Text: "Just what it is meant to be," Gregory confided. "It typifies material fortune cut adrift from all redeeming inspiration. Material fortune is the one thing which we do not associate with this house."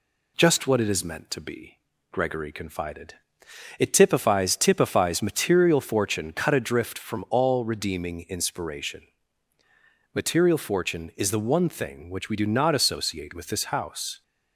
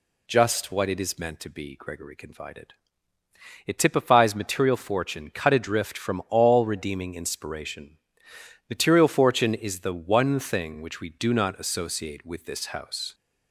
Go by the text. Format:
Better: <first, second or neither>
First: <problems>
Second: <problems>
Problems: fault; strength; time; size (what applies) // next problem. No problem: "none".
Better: second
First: says "typifies" twice; at 4.5 s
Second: none